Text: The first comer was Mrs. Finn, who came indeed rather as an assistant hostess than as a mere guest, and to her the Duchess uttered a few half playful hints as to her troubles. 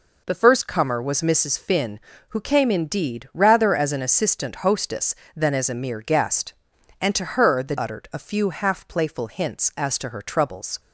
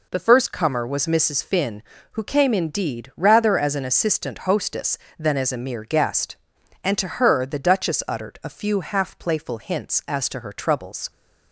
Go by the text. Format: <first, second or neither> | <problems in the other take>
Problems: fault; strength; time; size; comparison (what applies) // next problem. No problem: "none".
second | skips "Duchess"; at 7.7 s